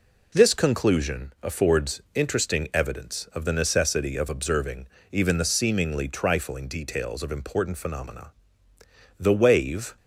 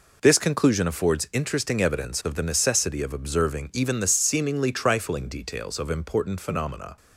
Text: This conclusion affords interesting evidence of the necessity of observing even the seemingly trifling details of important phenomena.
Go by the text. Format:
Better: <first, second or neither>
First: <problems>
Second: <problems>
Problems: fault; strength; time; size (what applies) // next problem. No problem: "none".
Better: second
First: pauses between "observing" and "even"; slight; at 4.8 s; 0.24 s long // goes on to say "The wave"; noticeable; from 9.1 s on; 0.78 s long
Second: none